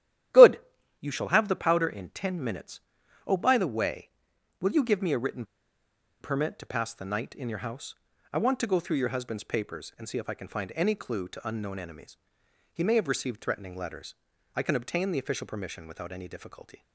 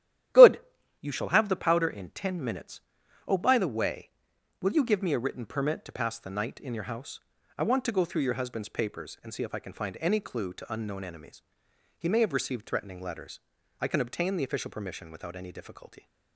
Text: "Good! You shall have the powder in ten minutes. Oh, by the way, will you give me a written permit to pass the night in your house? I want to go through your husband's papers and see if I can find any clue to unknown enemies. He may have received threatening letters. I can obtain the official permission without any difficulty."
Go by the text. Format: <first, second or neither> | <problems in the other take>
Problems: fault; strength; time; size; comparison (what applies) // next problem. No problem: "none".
second | starts louder than the rest; strong; until 1.7 s; 12 dB; strong in the second // pauses between "written" and "permit"; noticeable; at 5.4 s; 0.77 s long